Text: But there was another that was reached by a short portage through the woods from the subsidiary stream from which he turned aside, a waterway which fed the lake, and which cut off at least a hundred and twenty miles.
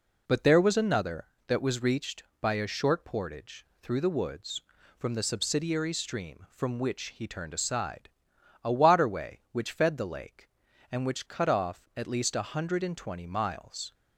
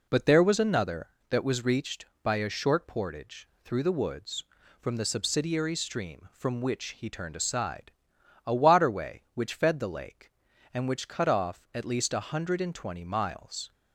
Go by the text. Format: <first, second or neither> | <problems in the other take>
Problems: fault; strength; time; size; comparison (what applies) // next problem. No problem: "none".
neither | pauses between "portage" and "through"; slight; the same in both